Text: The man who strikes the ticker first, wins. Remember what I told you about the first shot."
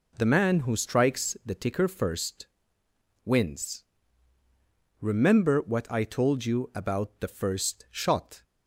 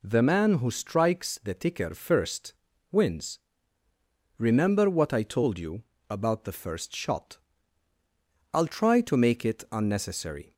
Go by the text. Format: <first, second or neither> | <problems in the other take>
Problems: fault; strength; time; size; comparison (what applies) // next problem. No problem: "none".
first | pauses between "you" and "about"; slight; at 5.8 s; 0.24 s long // goes on to say "I'll try to make it unnecessary"; strong; from 8.5 s on; 2.0 s long